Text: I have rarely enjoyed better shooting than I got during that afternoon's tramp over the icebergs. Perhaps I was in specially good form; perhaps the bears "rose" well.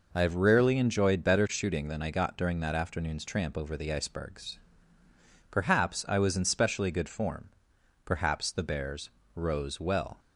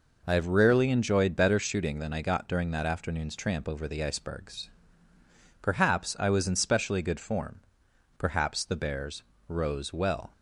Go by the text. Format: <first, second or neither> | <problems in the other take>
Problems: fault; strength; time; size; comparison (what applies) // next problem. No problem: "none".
neither | pauses between "bears" and "rose"; slight; the same in both